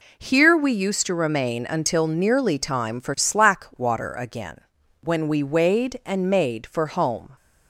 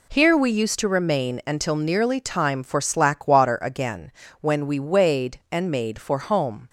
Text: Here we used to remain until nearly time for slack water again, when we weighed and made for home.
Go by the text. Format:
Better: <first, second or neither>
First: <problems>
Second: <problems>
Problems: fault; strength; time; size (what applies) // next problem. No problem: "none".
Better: neither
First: none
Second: none